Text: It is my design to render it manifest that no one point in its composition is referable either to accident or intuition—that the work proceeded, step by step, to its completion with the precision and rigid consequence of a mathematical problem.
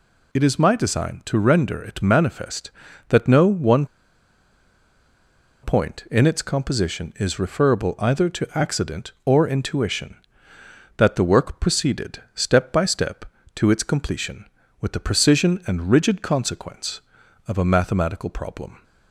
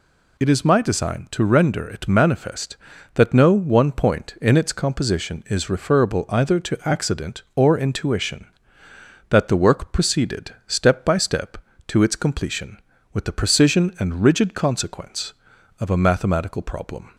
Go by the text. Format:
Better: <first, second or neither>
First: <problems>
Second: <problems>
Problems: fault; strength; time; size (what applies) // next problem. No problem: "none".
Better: second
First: pauses between "one" and "point"; strong; at 3.8 s; 1.7 s long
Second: none